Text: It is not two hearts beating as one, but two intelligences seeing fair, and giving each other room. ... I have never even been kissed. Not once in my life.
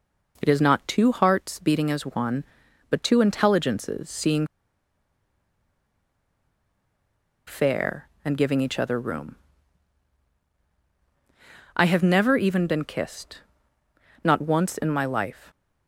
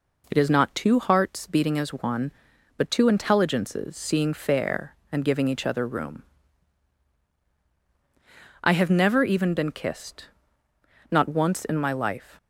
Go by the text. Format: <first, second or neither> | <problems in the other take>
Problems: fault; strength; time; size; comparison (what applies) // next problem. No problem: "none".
second | pauses between "seeing" and "fair"; strong; at 4.4 s; 3.0 s long